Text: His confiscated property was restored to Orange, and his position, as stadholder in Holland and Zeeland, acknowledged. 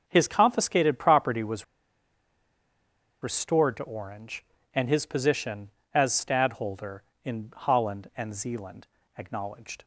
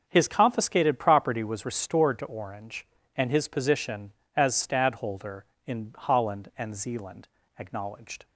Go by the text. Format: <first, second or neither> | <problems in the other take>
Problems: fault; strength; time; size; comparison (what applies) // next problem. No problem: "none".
second | starts louder than the rest; noticeable; until 1.0 s; 6 dB; noticeable in the second // pauses between "was" and "restored"; strong; at 1.6 s; 1.5 s long